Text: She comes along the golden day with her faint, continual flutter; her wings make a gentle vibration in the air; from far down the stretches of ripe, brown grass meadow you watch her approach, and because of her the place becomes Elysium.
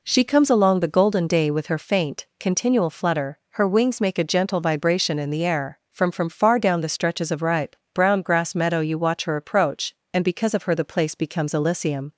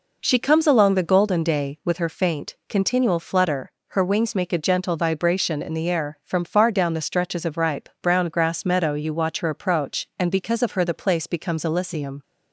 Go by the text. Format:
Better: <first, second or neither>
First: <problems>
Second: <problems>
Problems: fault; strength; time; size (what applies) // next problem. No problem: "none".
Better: second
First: says "from" twice; at 6.1 s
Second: none